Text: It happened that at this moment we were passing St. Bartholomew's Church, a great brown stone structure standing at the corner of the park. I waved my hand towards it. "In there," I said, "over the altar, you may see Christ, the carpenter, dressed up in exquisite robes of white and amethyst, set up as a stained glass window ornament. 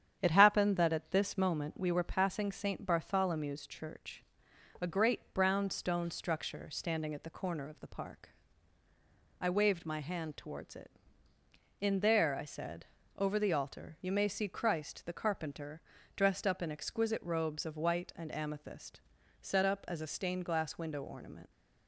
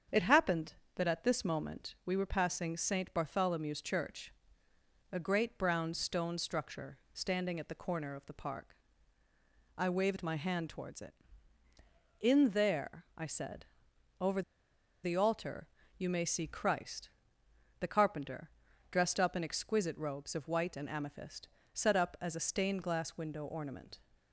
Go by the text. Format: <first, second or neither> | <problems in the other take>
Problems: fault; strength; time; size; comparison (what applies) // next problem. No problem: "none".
first | starts louder than the rest; strong; until 1.3 s; 8 dB; strong in the first // pauses between "structure" and "standing"; slight; at 6.9 s; 0.16 s long // pauses between "over" and "the"; noticeable; at 14.4 s; 0.62 s long